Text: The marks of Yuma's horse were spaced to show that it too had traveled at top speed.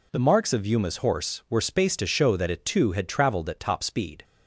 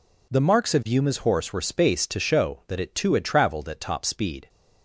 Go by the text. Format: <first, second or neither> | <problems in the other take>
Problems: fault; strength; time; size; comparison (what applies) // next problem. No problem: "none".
neither | none